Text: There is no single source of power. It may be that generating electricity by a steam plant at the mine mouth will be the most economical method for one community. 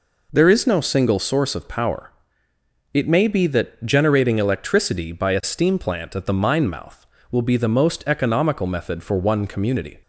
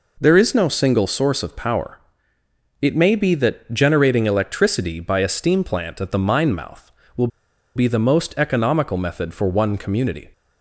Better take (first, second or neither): first